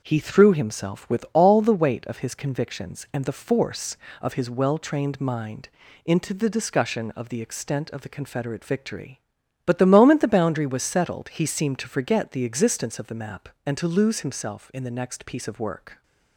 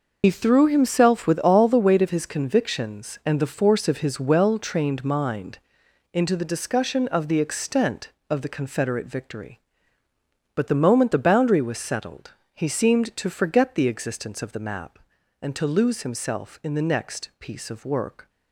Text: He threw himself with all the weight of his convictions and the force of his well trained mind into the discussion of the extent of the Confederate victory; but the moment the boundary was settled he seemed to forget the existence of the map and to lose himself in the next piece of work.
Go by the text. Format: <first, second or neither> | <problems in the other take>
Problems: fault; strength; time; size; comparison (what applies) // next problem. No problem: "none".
first | loses the start of "He"; at 0.2 s; 70 ms // pauses between "mind" and "into"; noticeable; at 5.5 s; 0.54 s long; slight in the first // pauses between "settled" and "he"; slight; at 12.3 s; 0.22 s long